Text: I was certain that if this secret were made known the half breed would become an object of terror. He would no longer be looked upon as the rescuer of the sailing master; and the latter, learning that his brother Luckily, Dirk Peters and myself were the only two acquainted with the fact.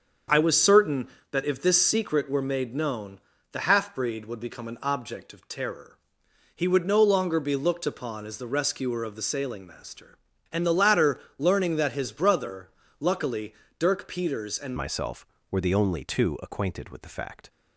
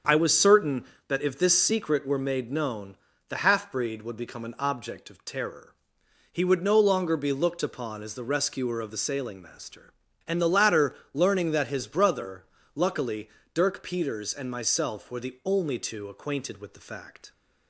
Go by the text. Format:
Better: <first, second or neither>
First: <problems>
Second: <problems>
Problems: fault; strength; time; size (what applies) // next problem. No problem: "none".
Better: second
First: starts louder than the rest; until 1.5 s; 7 dB // pauses between "known" and "the"; slight; at 3.1 s; 0.32 s long // pauses between "brother" and "Luckily"; slight; at 12.6 s; 0.30 s long // changes voice at "myself"; from 14.7 s on; 2.7 s long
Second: starts louder than the rest; until 1.3 s; 7 dB // pauses between "known" and "the"; slight; at 2.9 s; 0.32 s long // pauses between "brother" and "Luckily"; slight; at 12.4 s; 0.30 s long